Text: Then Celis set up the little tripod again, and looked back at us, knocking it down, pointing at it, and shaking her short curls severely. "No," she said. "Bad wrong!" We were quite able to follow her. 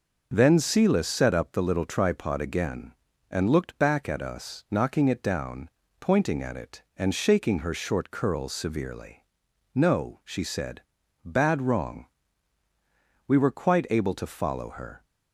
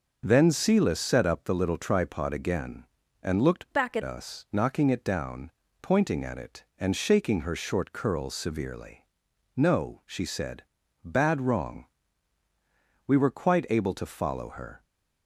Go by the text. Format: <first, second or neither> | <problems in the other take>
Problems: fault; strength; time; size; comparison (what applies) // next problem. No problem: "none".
first | changes voice from "back" to "at"; from 3.7 to 4.0 s; 0.3 s long